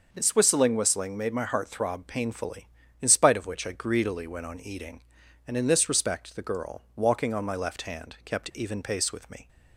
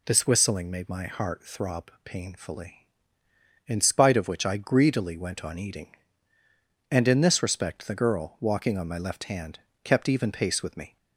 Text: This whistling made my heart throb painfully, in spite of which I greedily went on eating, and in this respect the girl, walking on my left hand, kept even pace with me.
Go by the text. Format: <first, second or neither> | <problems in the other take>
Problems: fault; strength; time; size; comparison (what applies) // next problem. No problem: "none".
second | says "whistling" twice; at 0.7 s